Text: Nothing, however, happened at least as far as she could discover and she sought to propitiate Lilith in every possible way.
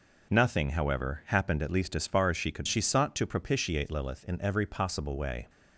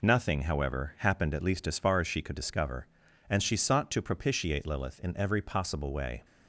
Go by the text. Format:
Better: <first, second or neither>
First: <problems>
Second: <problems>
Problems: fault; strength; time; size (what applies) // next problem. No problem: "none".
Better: second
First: skips "discover and"; at 2.6 s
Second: none